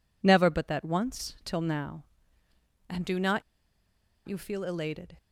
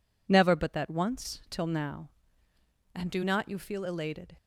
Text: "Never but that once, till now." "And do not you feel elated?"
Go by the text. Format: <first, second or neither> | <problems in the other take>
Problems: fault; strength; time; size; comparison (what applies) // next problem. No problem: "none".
second | pauses between "not" and "you"; noticeable; at 3.4 s; 0.85 s long